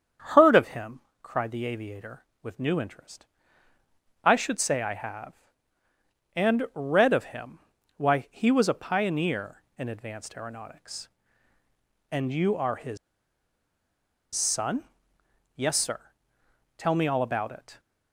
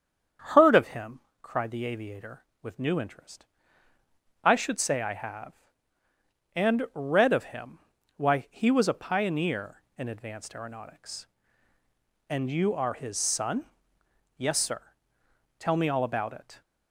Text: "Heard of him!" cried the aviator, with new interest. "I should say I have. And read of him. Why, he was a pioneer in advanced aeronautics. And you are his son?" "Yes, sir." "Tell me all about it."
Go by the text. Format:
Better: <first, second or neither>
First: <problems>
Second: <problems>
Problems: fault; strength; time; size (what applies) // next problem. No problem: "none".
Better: second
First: starts louder than the rest; strong; until 1.5 s; 8 dB // pauses between "his" and "son"; strong; at 12.9 s; 1.3 s long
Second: starts louder than the rest; strong; until 1.7 s; 8 dB